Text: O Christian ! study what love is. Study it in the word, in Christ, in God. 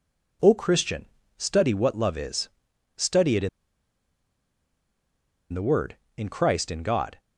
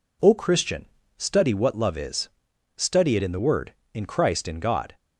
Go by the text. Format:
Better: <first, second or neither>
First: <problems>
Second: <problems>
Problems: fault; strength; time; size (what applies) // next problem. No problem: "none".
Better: second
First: pauses between "in" and "the"; strong; at 3.4 s; 2.0 s long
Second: none